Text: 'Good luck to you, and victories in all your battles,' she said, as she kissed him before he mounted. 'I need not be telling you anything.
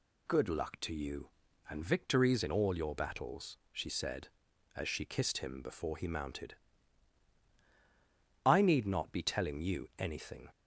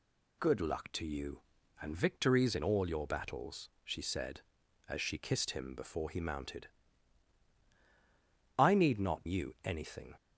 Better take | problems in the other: first | skips "be telling"; at 9.2 s

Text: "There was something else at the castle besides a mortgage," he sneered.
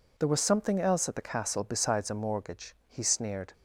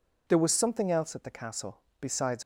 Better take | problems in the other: first | pauses between "castle" and "besides"; slight; at 1.8 s; 0.18 s long // stops before "a mortgage he sneered"; at 2.4 s

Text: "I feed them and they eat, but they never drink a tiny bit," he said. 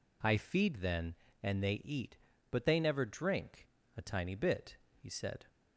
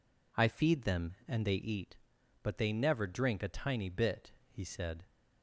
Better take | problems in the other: second | says "then" for "them"; at 0.8 s // pauses between "drink" and "a"; slight; at 3.6 s; 0.30 s long

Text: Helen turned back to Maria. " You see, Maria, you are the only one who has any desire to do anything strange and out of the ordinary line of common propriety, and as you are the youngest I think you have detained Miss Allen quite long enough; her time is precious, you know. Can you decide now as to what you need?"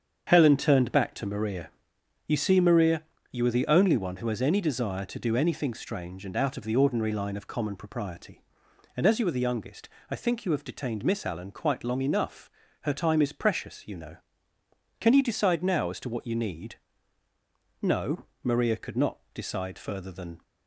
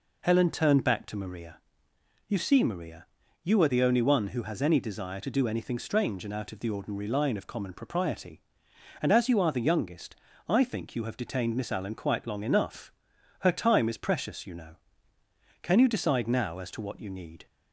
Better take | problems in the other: second | starts louder than the rest; strong; until 1.2 s; 7.5 dB // pauses between "youngest" and "I"; slight; at 9.8 s; 0.22 s long; slight in the second // goes on to say "No Maria could not decide further than"; strong; from 17.8 s on; 2.6 s long

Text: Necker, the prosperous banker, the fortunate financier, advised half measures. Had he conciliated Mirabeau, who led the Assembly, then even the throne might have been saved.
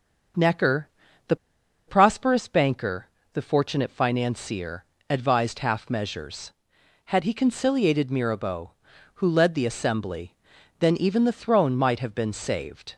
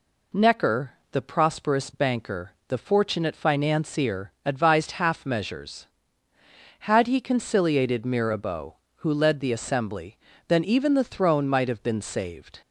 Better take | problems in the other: second | starts louder than the rest; until 2.3 s; 6 dB // pauses between "the" and "prosperous"; noticeable; at 1.3 s; 0.52 s long

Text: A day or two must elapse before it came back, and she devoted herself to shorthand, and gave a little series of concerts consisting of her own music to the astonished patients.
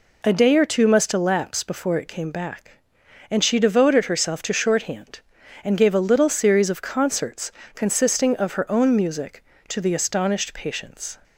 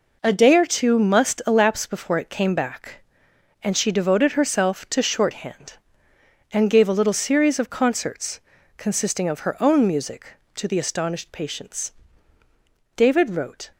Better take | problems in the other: first | pauses between "concerts" and "consisting"; slight; at 8.4 s; 0.36 s long; slight in the first // goes on to say "David wrote"; noticeable; from 12.9 s on; 0.74 s long

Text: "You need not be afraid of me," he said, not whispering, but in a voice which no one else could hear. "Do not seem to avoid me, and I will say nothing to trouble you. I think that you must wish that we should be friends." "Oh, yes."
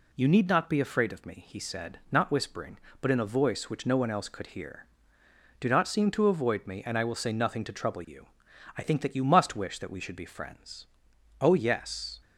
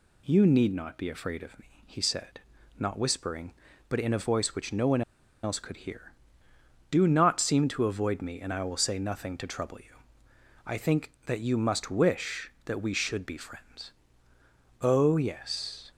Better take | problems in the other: first | pauses between "one" and "else"; at 5.0 s; 0.41 s long

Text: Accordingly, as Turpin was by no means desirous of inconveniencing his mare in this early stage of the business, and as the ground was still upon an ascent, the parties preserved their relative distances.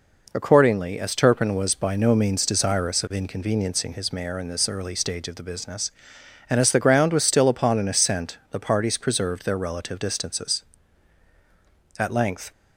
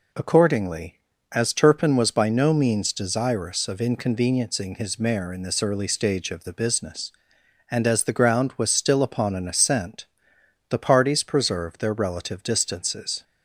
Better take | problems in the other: second | goes on to say "At length"; from 11.9 s on; 0.52 s long

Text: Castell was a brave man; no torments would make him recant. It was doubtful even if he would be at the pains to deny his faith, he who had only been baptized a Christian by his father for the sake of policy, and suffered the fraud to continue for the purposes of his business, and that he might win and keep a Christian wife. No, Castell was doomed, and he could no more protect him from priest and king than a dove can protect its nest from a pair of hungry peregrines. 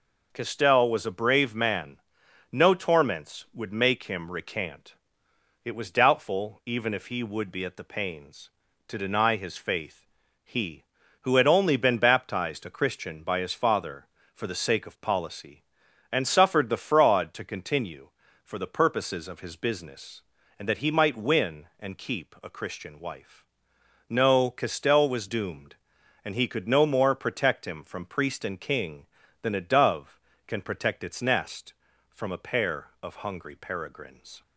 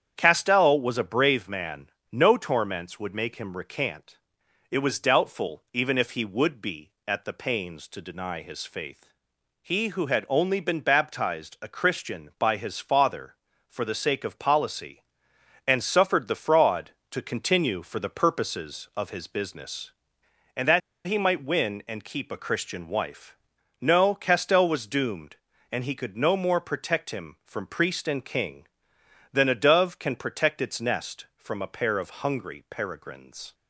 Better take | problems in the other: first | starts louder than the rest; strong; until 1.1 s; 8.5 dB // pauses between "that" and "he"; slight; at 20.8 s; 0.25 s long

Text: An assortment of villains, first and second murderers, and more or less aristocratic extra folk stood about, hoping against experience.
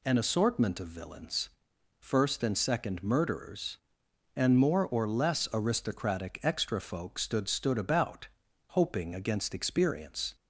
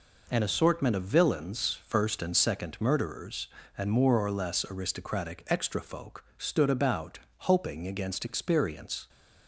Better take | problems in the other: second | says "stood" twice; at 7.4 s

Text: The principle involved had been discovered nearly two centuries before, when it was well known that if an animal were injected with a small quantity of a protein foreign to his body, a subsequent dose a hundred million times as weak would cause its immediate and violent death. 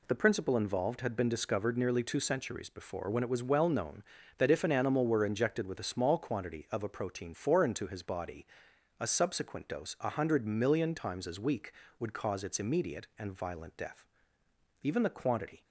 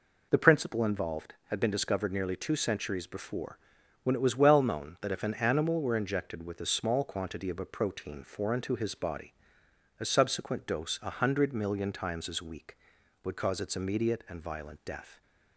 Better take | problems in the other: second | goes on to say "Even the quantity"; noticeable; from 14.8 s on; 0.82 s long

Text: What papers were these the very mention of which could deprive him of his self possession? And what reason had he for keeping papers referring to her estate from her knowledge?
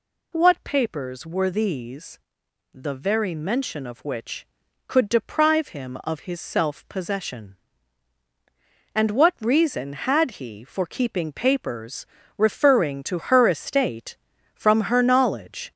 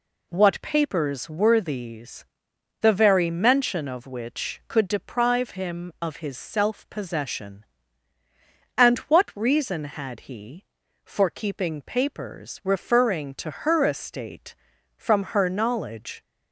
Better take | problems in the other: second | gets louder; noticeable; throughout; 4 dB // pauses between "these" and "the"; noticeable; at 2.1 s; 0.56 s long; noticeable in the second // pauses between "papers" and "referring"; slight; at 12.0 s; 0.32 s long

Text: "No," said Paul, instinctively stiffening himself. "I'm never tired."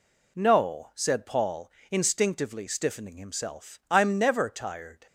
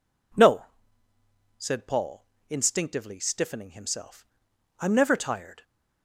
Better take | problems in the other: neither | none

